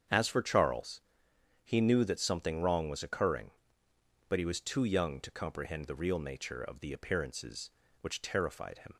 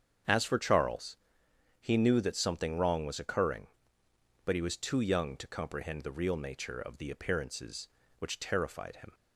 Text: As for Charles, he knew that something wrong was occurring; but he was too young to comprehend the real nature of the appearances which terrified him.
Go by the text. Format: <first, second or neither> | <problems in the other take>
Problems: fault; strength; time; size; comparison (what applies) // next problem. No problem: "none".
neither | starts louder than the rest; strong; the same in both